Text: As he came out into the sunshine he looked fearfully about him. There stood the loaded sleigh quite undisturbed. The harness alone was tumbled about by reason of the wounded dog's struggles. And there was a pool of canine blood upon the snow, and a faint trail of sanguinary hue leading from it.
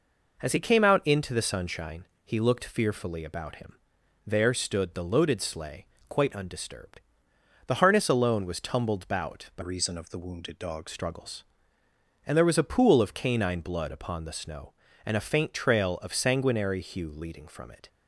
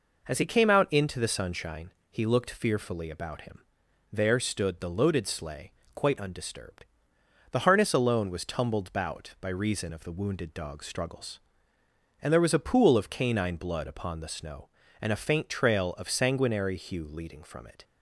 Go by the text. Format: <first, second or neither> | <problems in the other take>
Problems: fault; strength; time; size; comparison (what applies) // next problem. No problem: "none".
second | pauses between "sunshine" and "he"; slight; at 2.0 s; 0.18 s long; slight in the second // pauses between "sleigh" and "quite"; slight; at 5.8 s; 0.24 s long; slight in the second // changes voice from "reason" to "dog's"; from 9.6 to 10.8 s; 1.2 s long